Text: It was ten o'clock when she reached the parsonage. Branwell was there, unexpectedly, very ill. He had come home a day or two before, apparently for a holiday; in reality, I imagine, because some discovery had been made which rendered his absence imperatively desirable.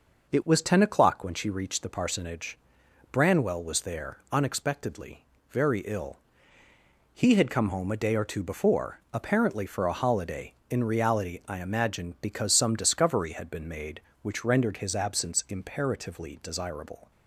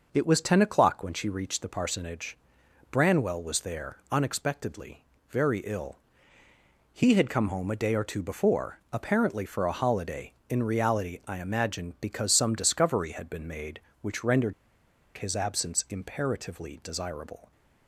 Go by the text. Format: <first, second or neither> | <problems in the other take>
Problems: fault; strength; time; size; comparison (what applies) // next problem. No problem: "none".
first | pauses between "rendered" and "his"; noticeable; at 14.5 s; 0.63 s long